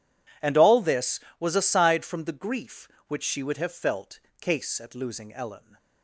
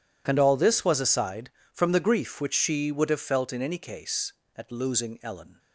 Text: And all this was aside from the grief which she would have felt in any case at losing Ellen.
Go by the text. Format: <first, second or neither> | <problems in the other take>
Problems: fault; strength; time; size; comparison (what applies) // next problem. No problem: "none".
second | skips "in any"; at 4.2 s